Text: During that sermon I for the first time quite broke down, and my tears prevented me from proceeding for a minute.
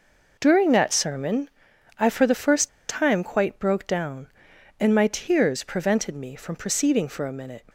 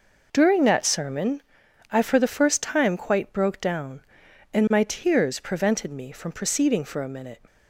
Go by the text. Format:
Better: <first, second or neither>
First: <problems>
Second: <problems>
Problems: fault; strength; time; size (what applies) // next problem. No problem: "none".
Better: second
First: pauses between "sermon" and "I"; noticeable; at 1.4 s; 0.48 s long // pauses between "first" and "time"; slight; at 2.6 s; 0.19 s long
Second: pauses between "sermon" and "I"; noticeable; at 1.4 s; 0.48 s long